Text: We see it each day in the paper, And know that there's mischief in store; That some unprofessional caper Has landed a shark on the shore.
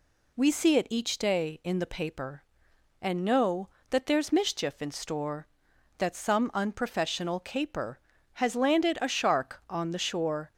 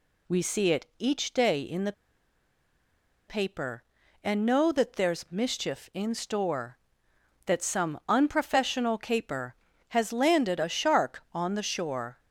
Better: first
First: none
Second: pauses between "the" and "paper"; strong; at 1.9 s; 1.3 s long

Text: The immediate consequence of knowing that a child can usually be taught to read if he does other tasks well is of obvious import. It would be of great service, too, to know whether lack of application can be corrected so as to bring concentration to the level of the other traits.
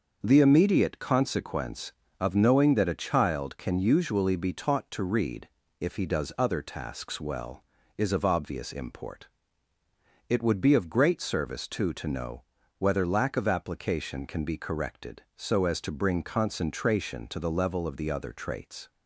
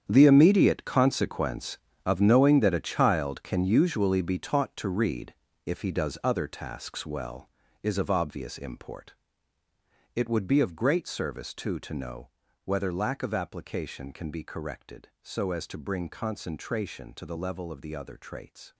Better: first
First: starts louder than the rest; until 1.2 s; 6.5 dB // pauses between "read" and "if"; slight; at 5.4 s; 0.30 s long // pauses between "know" and "whether"; slight; at 12.4 s; 0.34 s long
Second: gets quieter; strong; throughout; 13.5 dB // starts louder than the rest; strong; until 1.0 s; 8.5 dB // pauses between "read" and "if"; slight; at 5.3 s; 0.30 s long // pauses between "know" and "whether"; slight; at 12.2 s; 0.34 s long

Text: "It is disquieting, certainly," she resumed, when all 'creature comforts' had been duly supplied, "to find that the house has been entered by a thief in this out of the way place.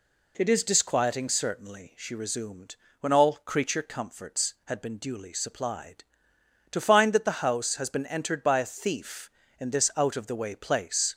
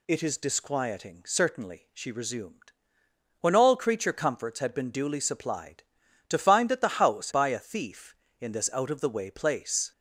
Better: first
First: none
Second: skips "has been entered"; at 7.3 s

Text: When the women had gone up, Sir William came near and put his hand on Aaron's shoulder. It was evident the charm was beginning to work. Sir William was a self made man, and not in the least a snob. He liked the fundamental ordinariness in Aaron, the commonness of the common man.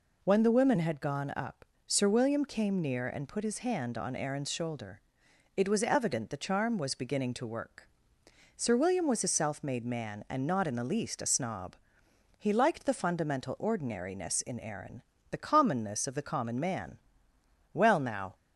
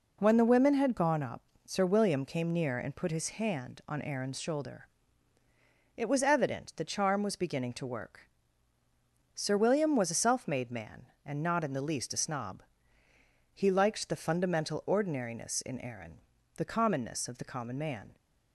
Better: second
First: goes on to say "Well now"; noticeable; from 17.7 s on; 0.62 s long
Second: none

